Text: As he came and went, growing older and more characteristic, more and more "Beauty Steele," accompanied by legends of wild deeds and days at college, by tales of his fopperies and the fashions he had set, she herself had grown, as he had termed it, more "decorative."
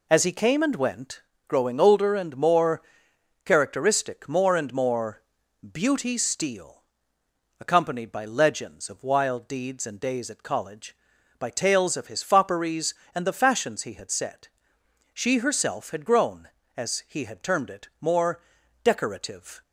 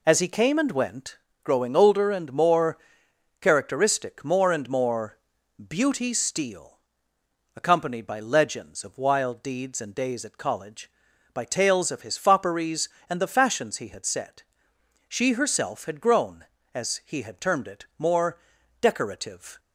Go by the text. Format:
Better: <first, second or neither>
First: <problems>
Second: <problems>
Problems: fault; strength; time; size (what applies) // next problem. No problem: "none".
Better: neither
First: pauses between "more" and "characteristic"; noticeable; at 2.8 s; 0.62 s long // pauses between "more" and "Beauty"; noticeable; at 5.2 s; 0.50 s long // pauses between "more" and "decorative"; at 18.3 s; 0.44 s long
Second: pauses between "more" and "characteristic"; noticeable; at 2.7 s; 0.62 s long // pauses between "more" and "Beauty"; noticeable; at 5.1 s; 0.50 s long // pauses between "more" and "decorative"; at 18.3 s; 0.44 s long